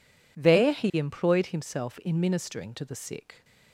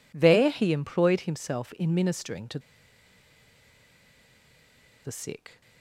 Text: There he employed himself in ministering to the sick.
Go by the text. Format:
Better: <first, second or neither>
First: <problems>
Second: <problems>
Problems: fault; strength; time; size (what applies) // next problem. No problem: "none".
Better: first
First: none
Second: pauses between "to" and "the"; strong; at 2.6 s; 2.4 s long